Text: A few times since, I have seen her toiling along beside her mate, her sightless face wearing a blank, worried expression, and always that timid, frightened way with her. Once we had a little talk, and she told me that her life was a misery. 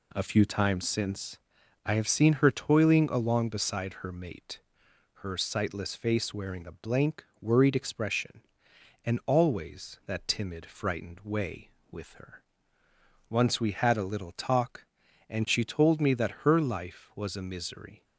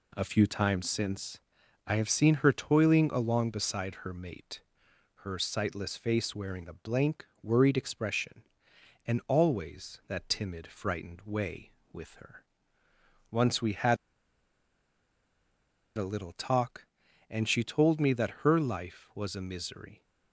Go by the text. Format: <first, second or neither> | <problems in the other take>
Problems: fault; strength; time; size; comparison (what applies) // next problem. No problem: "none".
first | pauses between "had" and "a"; strong; at 13.9 s; 1.9 s long